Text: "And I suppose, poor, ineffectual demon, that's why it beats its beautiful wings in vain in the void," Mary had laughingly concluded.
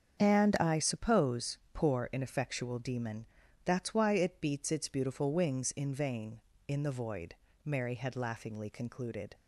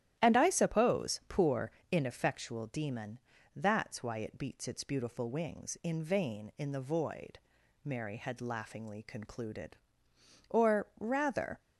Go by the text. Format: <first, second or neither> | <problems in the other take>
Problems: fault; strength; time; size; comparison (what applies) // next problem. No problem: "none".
first | starts louder than the rest; strong; until 1.2 s; 12 dB; strong in the first // goes on to say "Or rather"; noticeable; from 10.4 s on; 1.1 s long